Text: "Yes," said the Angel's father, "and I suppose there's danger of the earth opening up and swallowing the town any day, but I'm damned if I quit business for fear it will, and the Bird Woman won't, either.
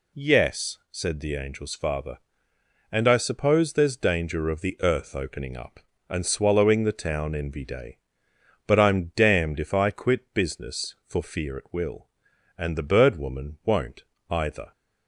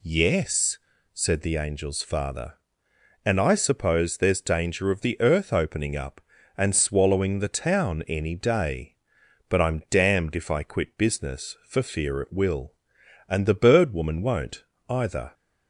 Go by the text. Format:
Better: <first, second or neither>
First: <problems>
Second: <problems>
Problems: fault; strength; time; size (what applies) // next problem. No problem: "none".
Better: second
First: says "envy" for "any"; at 7.3 s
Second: none